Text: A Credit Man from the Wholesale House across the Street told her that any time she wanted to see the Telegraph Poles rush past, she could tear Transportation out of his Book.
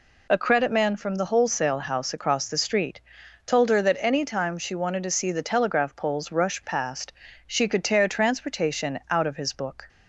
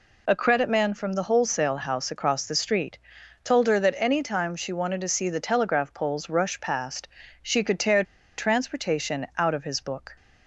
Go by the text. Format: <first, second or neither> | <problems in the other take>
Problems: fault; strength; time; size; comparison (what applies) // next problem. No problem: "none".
first | pauses between "Street" and "told"; noticeable; at 2.9 s; 0.48 s long; noticeable in the first // pauses between "tear" and "Transportation"; slight; at 8.0 s; 0.34 s long